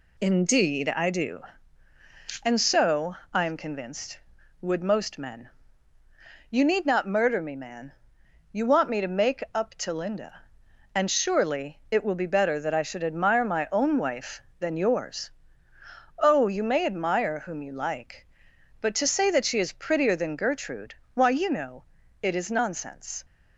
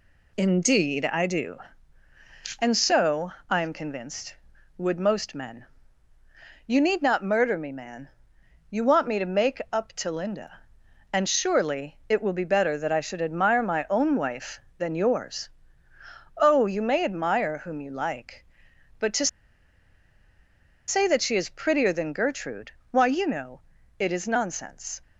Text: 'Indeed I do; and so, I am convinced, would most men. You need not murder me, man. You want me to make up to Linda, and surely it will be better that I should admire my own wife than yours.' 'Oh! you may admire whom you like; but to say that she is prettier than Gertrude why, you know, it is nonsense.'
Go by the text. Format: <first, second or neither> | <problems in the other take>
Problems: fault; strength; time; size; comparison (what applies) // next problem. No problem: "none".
first | pauses between "to" and "say"; strong; at 19.2 s; 1.6 s long // pauses between "Gertrude" and "why"; slight; at 22.7 s; 0.20 s long; slight in the first